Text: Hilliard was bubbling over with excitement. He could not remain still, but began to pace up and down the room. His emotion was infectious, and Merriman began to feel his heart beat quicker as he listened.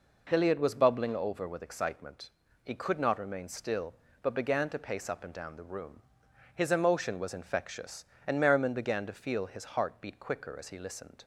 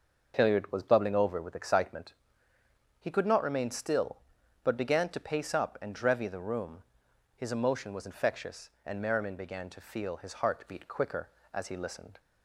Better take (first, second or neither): first